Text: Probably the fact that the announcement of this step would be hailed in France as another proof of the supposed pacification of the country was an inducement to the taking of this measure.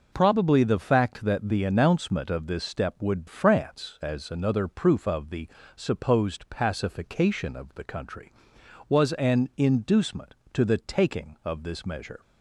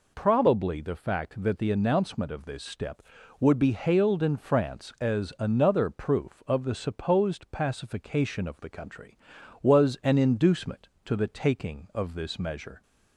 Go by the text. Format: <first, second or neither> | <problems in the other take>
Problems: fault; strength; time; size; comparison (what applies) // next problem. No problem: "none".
second | skips "be hailed in"; at 3.2 s // pauses between "the" and "supposed"; slight; at 5.4 s; 0.26 s long